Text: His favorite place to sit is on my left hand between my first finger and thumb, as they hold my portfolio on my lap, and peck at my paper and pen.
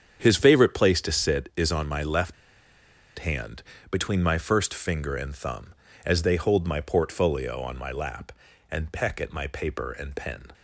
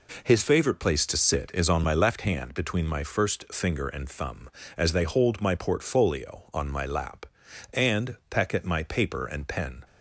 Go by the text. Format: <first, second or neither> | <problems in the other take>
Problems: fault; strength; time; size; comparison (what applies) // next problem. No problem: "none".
second | starts louder than the rest; strong; until 1.2 s; 8 dB // pauses between "left" and "hand"; noticeable; at 2.3 s; 0.93 s long // pauses between "hand" and "between"; slight; at 3.6 s; 0.30 s long